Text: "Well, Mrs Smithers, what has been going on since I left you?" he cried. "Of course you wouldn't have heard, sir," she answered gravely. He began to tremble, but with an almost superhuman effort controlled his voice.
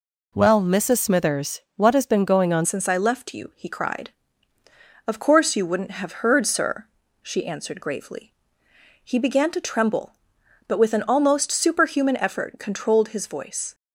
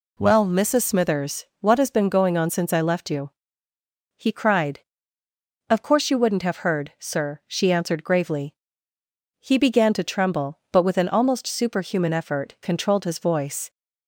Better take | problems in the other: second | changes voice at "since"; from 2.6 s on; 11.1 s long

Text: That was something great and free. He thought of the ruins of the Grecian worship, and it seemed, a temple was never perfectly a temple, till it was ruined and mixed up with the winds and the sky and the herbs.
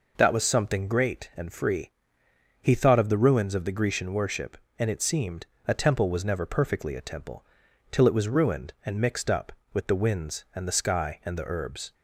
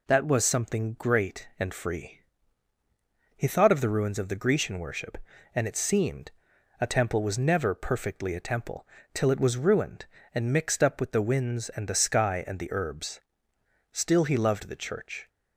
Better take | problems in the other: first | goes on to say "Still he loved the Church"; from 13.9 s on; 1.3 s long

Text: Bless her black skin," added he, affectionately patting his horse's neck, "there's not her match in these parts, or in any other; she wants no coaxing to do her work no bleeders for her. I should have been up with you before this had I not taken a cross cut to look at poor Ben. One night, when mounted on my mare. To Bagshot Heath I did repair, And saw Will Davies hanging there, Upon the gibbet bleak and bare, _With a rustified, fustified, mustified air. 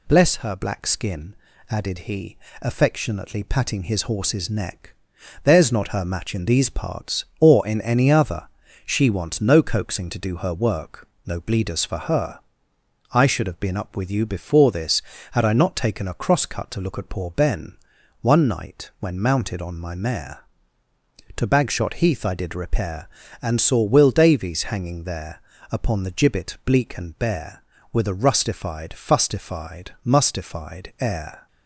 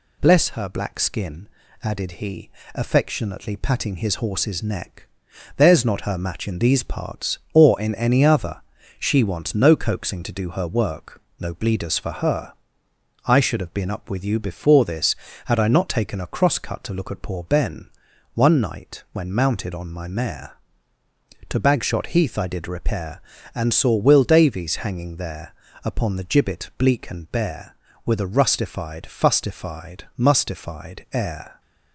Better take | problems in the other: neither | pauses between "work" and "no"; slight; the same in both

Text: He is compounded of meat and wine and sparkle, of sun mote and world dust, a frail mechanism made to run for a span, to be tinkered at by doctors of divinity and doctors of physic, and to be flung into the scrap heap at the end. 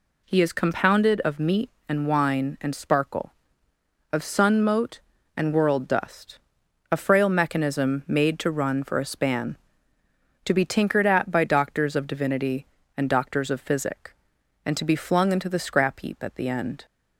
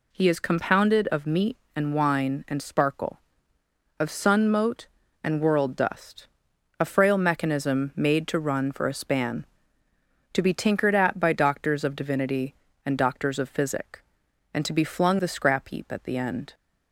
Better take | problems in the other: first | skips "into"; at 15.1 s

